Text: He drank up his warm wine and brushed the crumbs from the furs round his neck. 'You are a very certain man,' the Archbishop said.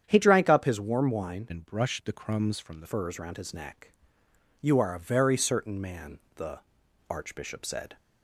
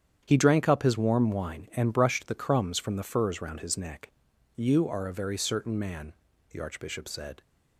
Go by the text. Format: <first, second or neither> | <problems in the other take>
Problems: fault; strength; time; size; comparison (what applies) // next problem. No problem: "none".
second | starts louder than the rest; strong; until 1.0 s; 9 dB; strong in the second // changes voice from "and" to "the"; from 1.4 to 2.8 s; 1.4 s long // pauses between "the" and "Archbishop"; noticeable; at 6.6 s; 0.48 s long